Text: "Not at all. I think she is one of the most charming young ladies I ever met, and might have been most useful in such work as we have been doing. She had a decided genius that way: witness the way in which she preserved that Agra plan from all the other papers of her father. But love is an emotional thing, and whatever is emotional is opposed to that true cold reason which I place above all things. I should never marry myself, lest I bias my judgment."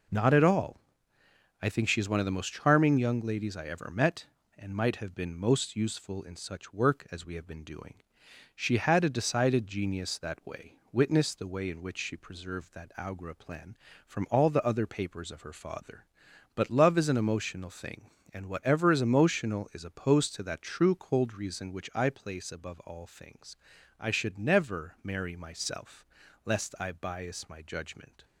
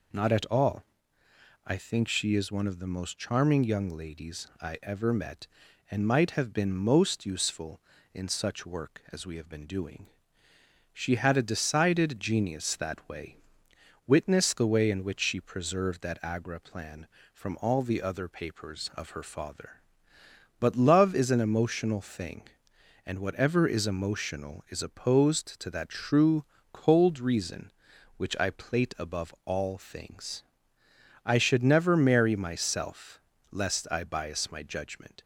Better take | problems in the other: first | pauses between "true" and "cold"; slight; at 26.4 s; 0.28 s long // says "plate" for "place"; at 28.5 s

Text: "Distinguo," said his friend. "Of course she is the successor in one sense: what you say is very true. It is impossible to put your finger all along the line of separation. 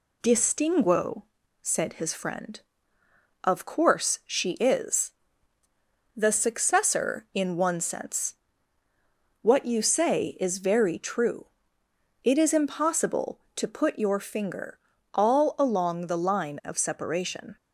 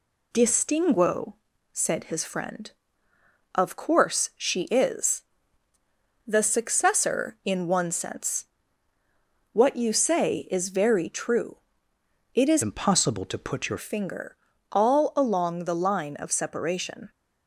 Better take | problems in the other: first | pauses between "is" and "the"; at 5.2 s; 1.0 s long; also in the first // changes voice from "impossible" to "your"; from 12.6 to 13.7 s; 1.1 s long // pauses between "finger" and "all"; slight; at 14.3 s; 0.36 s long; slight in the first

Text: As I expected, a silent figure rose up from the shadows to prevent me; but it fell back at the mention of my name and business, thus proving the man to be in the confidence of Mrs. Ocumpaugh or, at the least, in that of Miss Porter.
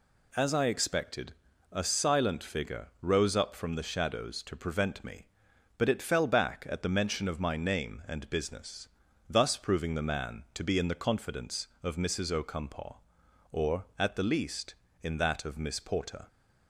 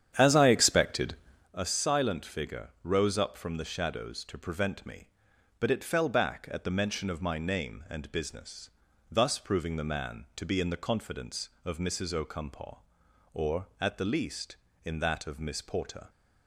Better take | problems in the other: first | starts louder than the rest; strong; until 1.5 s; 9 dB

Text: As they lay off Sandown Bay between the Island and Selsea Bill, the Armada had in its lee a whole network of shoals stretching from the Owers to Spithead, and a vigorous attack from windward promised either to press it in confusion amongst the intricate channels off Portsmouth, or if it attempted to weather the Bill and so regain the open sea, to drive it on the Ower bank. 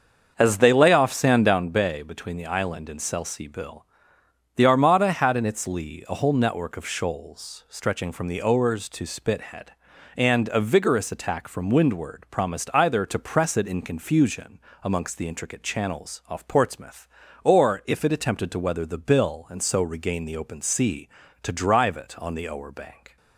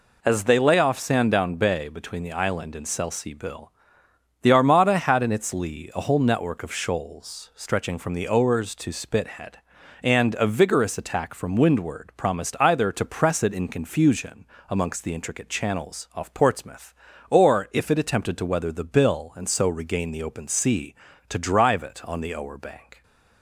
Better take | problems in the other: second | starts louder than the rest; until 1.7 s; 7 dB // pauses between "confusion" and "amongst"; slight; at 14.5 s; 0.24 s long; slight in the second

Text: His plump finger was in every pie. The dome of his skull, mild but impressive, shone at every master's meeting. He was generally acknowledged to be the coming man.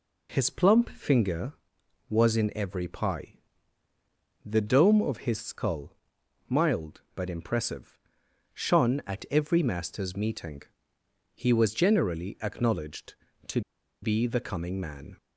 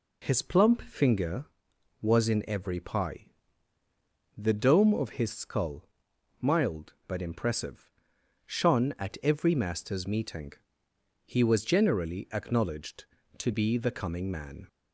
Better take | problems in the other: second | pauses between "to" and "be"; at 13.6 s; 0.41 s long

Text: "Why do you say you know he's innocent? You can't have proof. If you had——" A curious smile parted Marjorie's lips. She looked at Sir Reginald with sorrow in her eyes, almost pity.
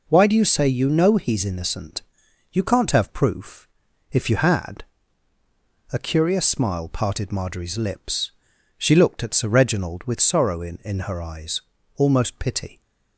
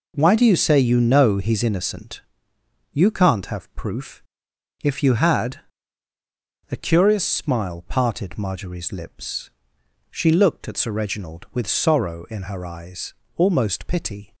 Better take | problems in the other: second | says "in" twice; at 10.8 s

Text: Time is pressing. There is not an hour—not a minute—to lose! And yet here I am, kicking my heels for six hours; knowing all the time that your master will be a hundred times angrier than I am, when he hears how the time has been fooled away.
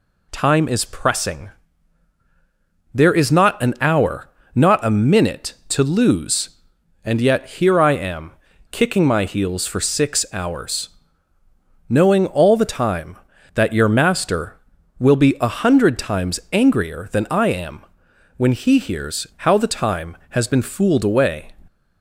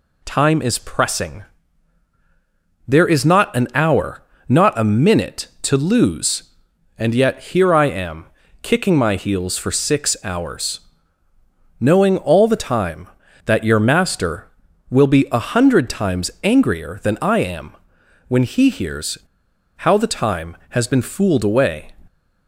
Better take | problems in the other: first | pauses between "hears" and "how"; noticeable; at 19.1 s; 0.58 s long

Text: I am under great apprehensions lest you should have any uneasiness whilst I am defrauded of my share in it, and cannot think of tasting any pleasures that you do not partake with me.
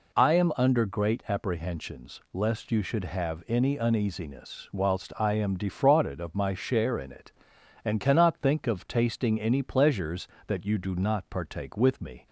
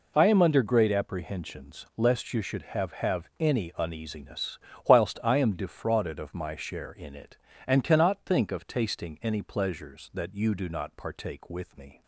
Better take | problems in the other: first | says "have" twice; at 2.9 s // pauses between "uneasiness" and "whilst"; slight; at 4.5 s; 0.28 s long

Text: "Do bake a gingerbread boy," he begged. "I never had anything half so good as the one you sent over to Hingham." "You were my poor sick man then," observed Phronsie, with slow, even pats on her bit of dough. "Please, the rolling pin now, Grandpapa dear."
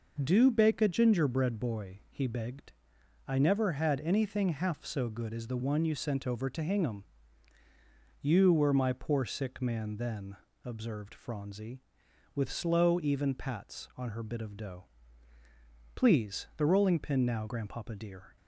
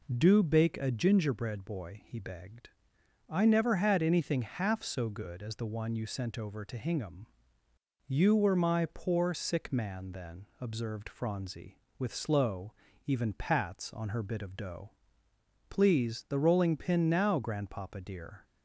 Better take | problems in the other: neither | none

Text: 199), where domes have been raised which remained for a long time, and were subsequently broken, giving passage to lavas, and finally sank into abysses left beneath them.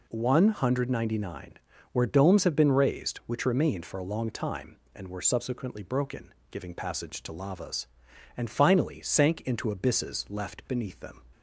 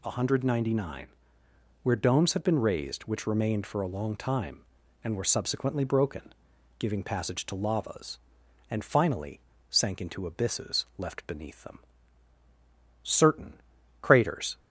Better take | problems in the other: first | pauses between "finally" and "sank"; slight; at 9.4 s; 0.30 s long // goes on to say "Certain craters"; from 13.0 s on; 1.5 s long

